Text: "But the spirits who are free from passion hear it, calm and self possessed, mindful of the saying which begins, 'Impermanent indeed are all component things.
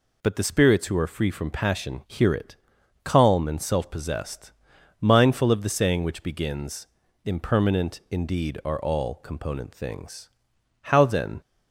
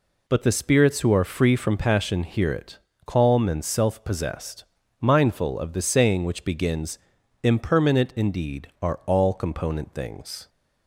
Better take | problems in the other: second | goes on to say "How then"; from 10.8 s on; 0.58 s long

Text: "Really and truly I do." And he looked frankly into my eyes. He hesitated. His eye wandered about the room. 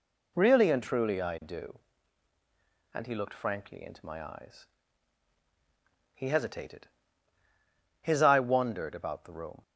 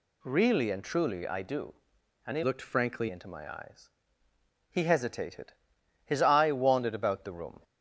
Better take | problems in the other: first | changes voice from "looked" to "frankly"; from 2.4 to 3.0 s; 0.6 s long

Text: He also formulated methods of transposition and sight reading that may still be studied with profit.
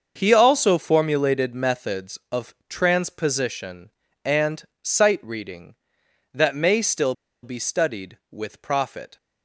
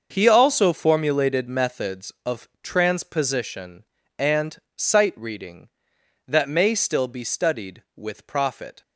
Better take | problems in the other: second | starts louder than the rest; until 1.1 s; 6.5 dB; also in the second // pauses between "of" and "transposition"; slight; at 2.5 s; 0.16 s long; slight in the second // pauses between "and" and "sight"; slight; at 4.6 s; 0.16 s long; slight in the second // pauses between "still" and "be"; slight; at 7.1 s; 0.30 s long

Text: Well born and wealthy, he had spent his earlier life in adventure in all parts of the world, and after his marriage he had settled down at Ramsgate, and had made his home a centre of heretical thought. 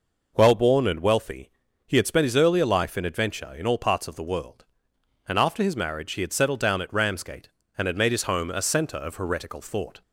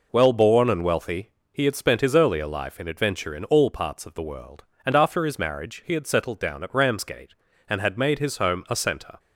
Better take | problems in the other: first | stops before "of heretical thought"; at 9.1 s

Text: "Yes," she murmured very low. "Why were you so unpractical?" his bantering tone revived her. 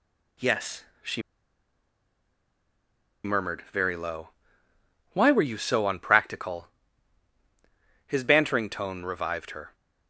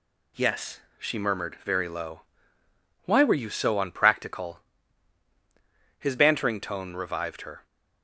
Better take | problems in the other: second | pauses between "she" and "murmured"; strong; at 1.2 s; 2.0 s long

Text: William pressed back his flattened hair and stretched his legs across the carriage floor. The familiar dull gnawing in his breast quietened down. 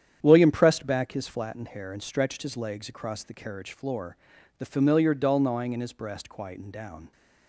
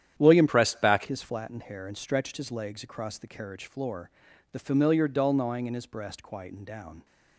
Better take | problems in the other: first | starts louder than the rest; strong; until 1.2 s; 10 dB; strong in the first // changes voice from "pressed" to "back"; from 0.4 to 1.0 s; 0.6 s long

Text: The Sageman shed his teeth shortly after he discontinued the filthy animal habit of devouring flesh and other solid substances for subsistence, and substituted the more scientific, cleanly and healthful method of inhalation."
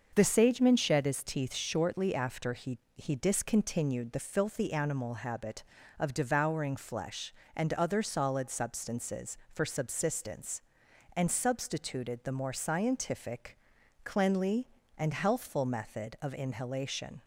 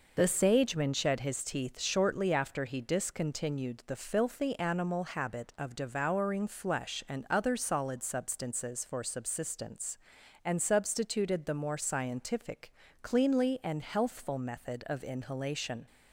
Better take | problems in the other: second | starts louder than the rest; until 1.1 s; 6 dB // says "he" twice; at 2.9 s

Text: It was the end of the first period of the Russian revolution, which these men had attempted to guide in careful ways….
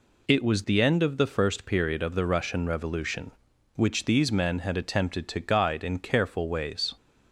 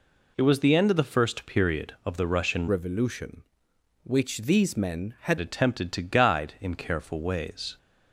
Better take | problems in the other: first | changes voice from "revolution" to "had"; from 2.6 to 5.3 s; 2.7 s long

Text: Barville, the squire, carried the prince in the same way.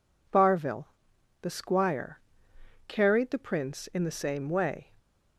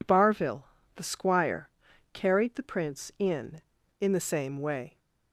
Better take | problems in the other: first | says "in" twice; at 4.0 s

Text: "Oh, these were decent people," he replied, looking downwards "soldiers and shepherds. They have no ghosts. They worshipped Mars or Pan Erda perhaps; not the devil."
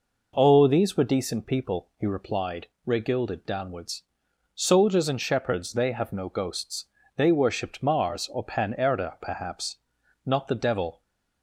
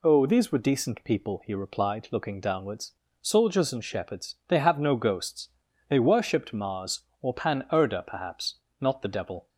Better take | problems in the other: second | says "regilded" for "looking"; at 2.8 s // pauses between "downwards" and "soldiers"; noticeable; at 4.0 s; 0.54 s long; slight in the second

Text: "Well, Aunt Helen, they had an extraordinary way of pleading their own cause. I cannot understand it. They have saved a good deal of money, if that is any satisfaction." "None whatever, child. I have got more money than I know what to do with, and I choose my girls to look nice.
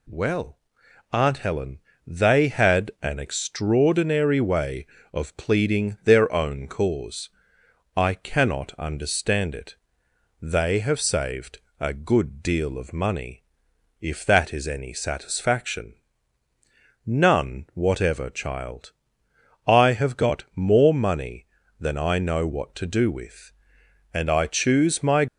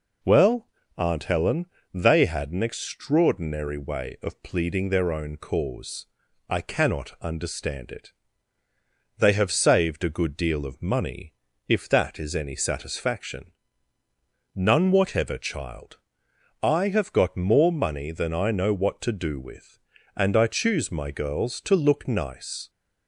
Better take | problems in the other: second | pauses between "saved" and "a"; slight; at 11.5 s; 0.20 s long // stops before "girls to look nice"; at 25.2 s

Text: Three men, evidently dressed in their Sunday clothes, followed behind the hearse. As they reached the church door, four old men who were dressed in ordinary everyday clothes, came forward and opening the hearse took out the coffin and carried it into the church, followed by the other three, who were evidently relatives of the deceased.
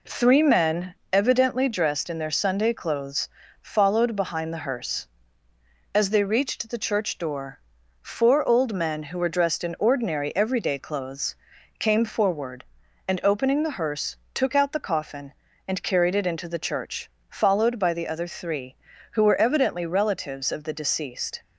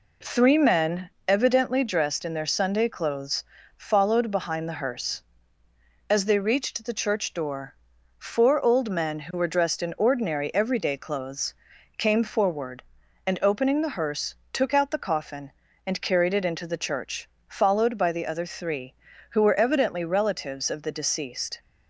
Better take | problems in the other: neither | pauses between "hearse" and "took"; slight; the same in both

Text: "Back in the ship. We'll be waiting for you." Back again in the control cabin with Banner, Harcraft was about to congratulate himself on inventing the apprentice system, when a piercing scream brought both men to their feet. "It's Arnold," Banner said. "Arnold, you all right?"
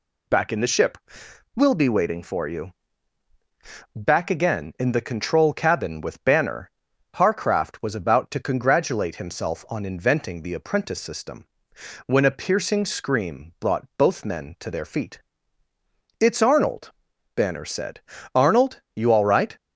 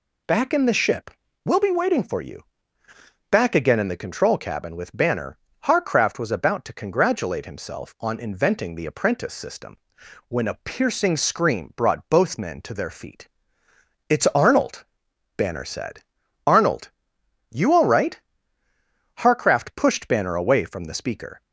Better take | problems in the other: first | goes on to say "Harcraft pushed Banner away from the speaker"; strong; from 19.1 s on; 2.2 s long

